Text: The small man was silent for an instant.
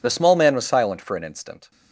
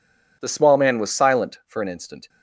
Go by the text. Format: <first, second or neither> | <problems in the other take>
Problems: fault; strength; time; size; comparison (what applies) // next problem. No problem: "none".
neither | none